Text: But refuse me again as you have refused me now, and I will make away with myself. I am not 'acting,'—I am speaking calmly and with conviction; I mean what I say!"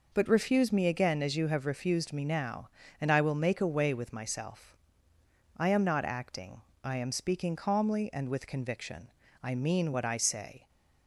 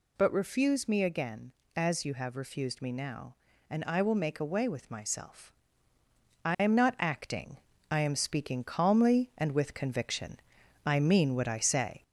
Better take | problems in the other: first | gets louder; slight; throughout; 2.5 dB

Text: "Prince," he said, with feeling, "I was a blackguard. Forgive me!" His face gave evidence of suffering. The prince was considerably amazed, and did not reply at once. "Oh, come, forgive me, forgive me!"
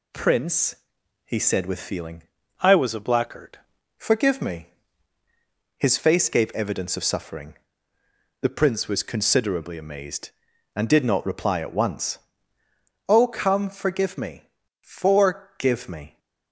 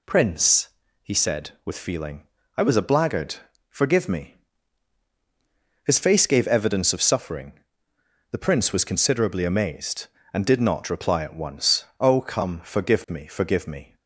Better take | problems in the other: second | changes voice from "I" to "blackguard"; from 2.6 to 3.5 s; 0.9 s long

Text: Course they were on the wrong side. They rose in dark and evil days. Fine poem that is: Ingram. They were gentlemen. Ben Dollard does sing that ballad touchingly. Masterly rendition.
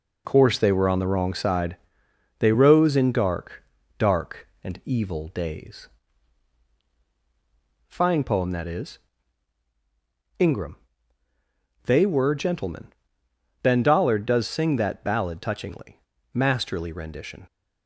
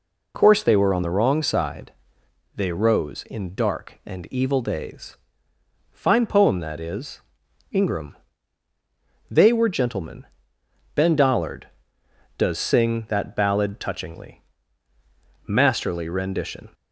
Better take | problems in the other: second | says "dark" twice; at 3.9 s

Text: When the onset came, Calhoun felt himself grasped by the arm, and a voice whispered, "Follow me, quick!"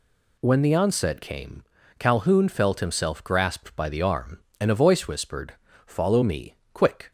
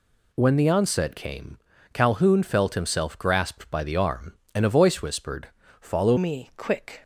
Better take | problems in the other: first | changes voice at "me"; from 6.1 s on; 0.9 s long

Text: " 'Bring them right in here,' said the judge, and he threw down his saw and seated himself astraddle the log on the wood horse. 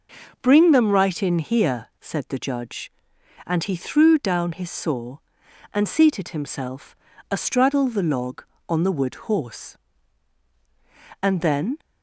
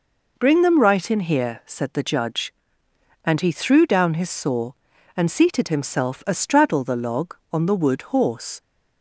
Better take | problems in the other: second | pauses between "himself" and "astraddle"; slight; at 6.9 s; 0.36 s long // goes on to say "And then"; from 11.2 s on; 0.56 s long

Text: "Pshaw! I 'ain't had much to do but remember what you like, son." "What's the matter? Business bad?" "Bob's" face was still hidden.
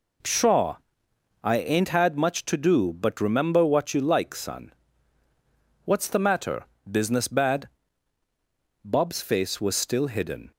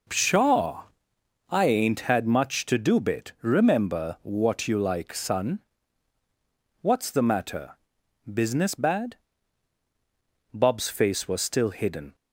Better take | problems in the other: first | says "bit" for "but"; at 3.0 s

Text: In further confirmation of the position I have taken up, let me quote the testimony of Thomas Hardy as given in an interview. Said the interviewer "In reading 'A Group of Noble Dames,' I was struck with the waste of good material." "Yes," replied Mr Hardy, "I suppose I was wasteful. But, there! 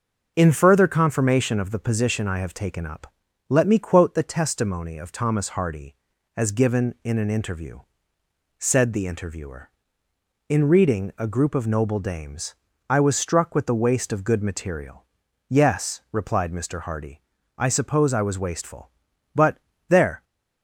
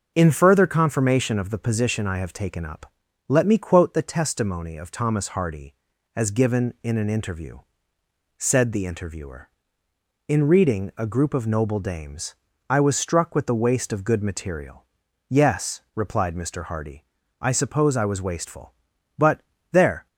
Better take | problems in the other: neither | starts louder than the rest; noticeable; the same in both

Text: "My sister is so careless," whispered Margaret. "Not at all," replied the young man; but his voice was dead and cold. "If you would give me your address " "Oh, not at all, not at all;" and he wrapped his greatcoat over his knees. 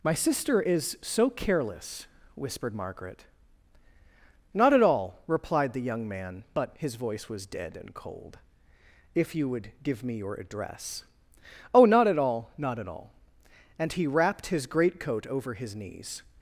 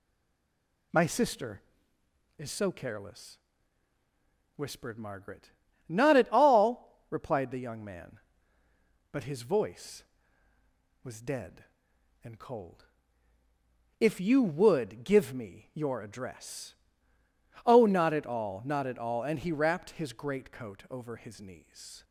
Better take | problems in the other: first | stays silent before the first word; slight; until 0.9 s; 0.9 s long

